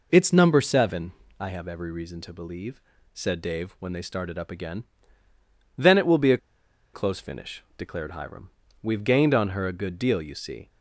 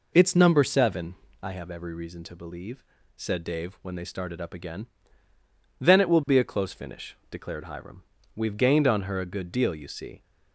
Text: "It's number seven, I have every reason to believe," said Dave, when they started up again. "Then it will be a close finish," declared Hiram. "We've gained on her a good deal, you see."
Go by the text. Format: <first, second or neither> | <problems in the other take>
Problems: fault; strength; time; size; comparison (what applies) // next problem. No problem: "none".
second | pauses between "a" and "close"; noticeable; at 6.3 s; 0.55 s long